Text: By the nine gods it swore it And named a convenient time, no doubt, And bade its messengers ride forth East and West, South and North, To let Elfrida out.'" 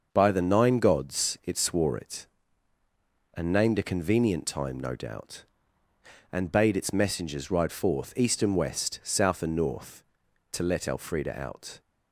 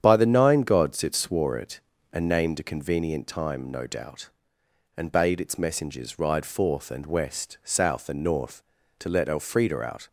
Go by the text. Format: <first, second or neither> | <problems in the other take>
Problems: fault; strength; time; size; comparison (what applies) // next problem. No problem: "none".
first | starts louder than the rest; strong; until 1.0 s; 9 dB; also in the first // skips "East"; at 6.9 s